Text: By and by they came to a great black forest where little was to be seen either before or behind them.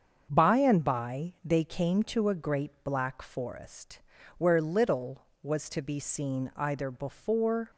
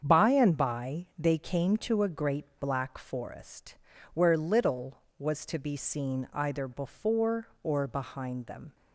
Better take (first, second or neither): second